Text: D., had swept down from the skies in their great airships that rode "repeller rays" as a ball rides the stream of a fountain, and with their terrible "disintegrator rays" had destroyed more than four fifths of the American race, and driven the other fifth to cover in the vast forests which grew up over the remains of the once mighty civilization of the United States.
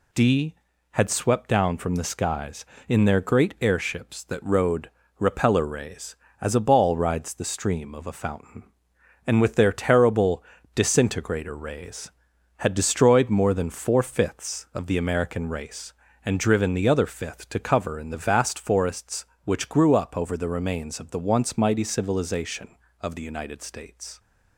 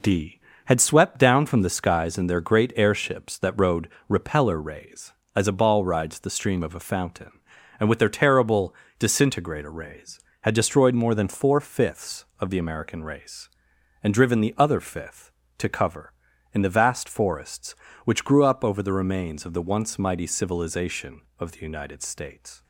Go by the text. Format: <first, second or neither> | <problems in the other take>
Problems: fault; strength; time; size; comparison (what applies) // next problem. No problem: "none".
neither | pauses between "rode" and "repeller"; slight; the same in both // pauses between "terrible" and "disintegrator"; slight; the same in both